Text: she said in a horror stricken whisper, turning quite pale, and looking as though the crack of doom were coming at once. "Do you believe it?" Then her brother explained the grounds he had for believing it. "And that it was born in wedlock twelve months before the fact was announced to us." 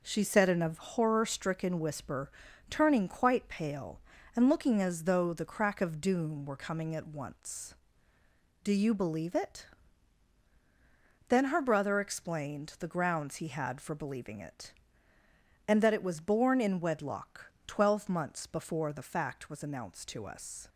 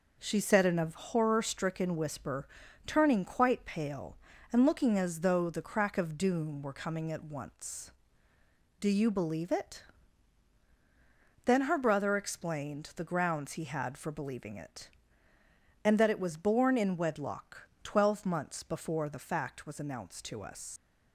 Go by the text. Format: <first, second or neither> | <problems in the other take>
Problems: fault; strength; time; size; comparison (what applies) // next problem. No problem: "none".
first | pauses between "wedlock" and "twelve"; slight; at 17.6 s; 0.16 s long; slight in the first // leaves "us" unfinished; at 20.7 s; 90 ms